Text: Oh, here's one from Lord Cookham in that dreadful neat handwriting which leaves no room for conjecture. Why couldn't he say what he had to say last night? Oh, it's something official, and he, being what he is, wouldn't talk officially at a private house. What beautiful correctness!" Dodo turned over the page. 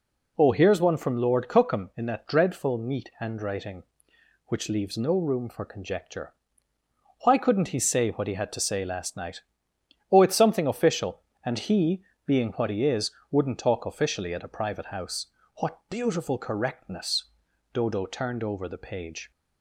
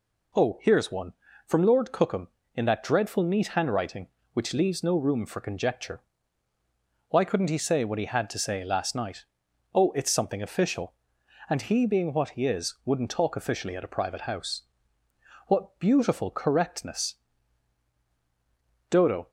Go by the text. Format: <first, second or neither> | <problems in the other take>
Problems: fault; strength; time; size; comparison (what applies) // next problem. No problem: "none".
first | stops before "turned over the page"; at 19.2 s